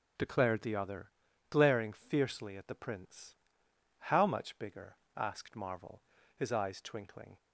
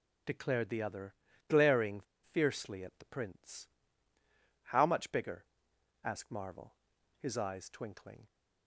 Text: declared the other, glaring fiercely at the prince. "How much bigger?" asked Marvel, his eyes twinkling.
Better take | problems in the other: first | pauses between "glaring" and "fiercely"; slight; at 2.0 s; 0.32 s long

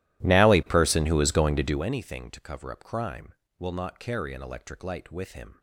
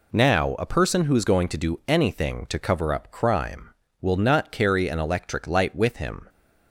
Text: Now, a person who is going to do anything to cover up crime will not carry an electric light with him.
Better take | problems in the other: second | starts louder than the rest; strong; until 1.9 s; 15 dB

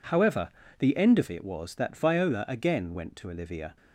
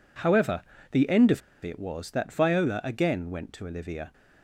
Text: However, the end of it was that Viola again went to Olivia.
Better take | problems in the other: first | pauses between "of" and "it"; slight; at 1.4 s; 0.24 s long

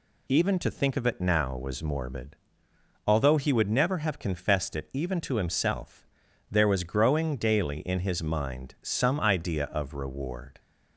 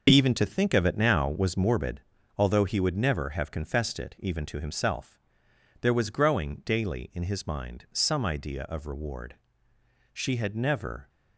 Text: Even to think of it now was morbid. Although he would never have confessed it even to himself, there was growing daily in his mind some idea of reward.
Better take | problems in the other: first | starts louder than the rest; until 1.1 s; 6 dB // goes on to say "She had never"; noticeable; from 10.1 s on; 0.94 s long

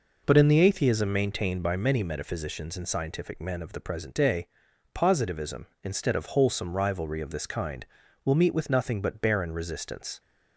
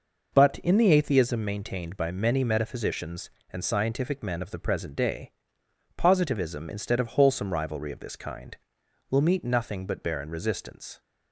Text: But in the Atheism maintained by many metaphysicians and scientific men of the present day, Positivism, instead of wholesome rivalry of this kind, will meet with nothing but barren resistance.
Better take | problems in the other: first | skips "with"; at 9.4 s

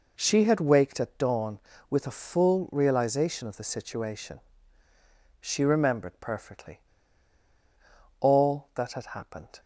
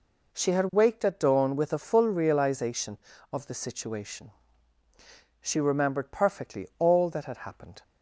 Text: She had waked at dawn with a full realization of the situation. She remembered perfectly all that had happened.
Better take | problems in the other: second | pauses between "perfectly" and "all"; strong; at 6.8 s; 1.4 s long

